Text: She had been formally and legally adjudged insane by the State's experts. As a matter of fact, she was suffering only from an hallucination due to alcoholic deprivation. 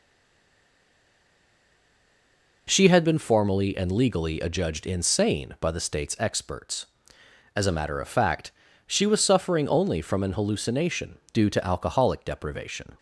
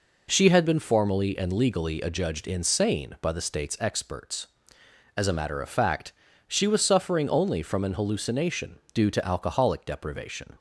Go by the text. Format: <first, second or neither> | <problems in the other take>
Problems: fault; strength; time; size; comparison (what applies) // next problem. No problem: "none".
second | stays silent before the first word; strong; until 2.6 s; 2.6 s long